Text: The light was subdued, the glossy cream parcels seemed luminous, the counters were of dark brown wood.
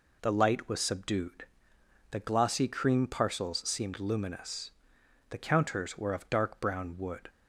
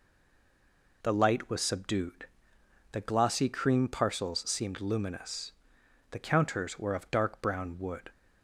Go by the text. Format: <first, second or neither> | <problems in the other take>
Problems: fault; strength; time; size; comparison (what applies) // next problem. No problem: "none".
first | stays silent before the first word; until 1.0 s; 1.0 s long